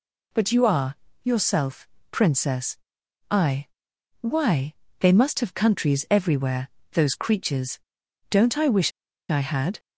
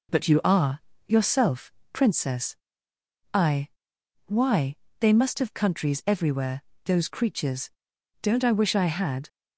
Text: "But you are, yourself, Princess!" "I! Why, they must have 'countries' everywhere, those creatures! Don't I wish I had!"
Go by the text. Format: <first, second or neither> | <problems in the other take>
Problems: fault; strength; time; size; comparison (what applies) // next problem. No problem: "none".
second | pauses between "wish" and "I"; at 8.9 s; 0.40 s long